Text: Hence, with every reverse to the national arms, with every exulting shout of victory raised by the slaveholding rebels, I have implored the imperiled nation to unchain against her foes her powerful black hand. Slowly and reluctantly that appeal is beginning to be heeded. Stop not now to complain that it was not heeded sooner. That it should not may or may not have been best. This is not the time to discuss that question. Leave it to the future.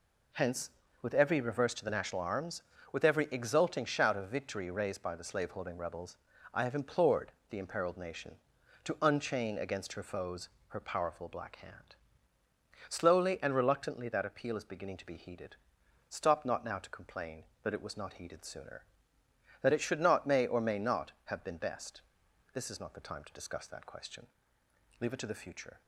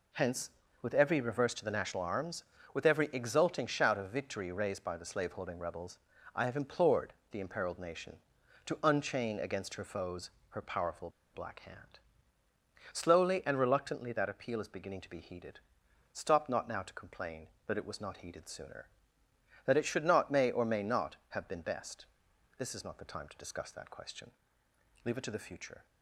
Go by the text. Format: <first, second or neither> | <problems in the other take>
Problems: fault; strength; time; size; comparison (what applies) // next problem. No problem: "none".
first | pauses between "implored" and "the"; slight; at 7.1 s; 0.18 s long; slight in the first // pauses between "foes" and "her"; slight; at 10.2 s; 0.20 s long; slight in the first // pauses between "powerful" and "black"; slight; at 11.0 s; 0.24 s long